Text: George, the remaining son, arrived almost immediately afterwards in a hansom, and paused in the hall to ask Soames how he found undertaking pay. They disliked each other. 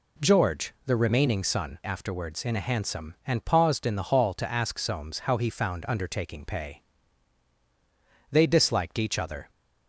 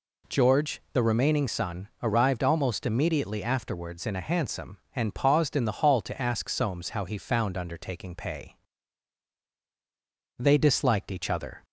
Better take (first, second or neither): second